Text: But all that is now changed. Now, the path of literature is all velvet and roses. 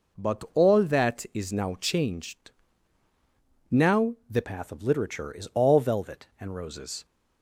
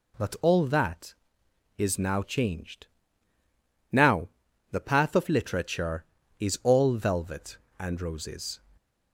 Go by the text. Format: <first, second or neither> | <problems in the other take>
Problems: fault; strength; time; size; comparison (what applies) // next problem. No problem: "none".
second | changes voice at "path"; from 4.4 s on; 2.6 s long